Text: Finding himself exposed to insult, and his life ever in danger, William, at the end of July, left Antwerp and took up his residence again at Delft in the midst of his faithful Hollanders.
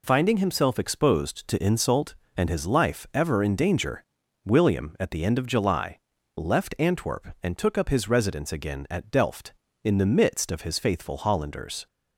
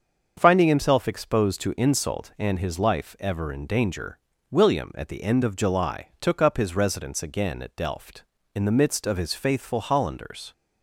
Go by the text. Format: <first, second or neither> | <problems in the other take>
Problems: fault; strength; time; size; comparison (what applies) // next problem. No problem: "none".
first | starts louder than the rest; until 1.3 s; 7 dB // skips "left Antwerp and"; at 6.1 s